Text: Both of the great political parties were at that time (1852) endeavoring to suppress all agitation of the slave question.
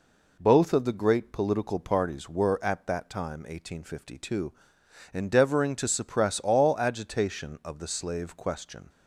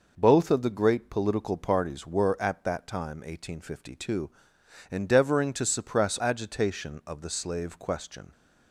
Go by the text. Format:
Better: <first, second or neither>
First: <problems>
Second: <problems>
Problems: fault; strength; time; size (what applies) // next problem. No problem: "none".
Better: first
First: none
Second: skips "all"; at 6.1 s